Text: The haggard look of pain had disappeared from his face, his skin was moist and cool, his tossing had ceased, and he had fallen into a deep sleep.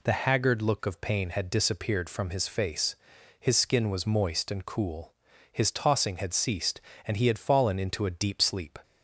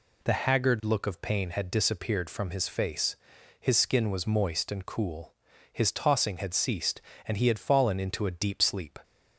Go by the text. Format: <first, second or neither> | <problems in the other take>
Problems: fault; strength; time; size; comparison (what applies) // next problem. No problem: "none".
neither | none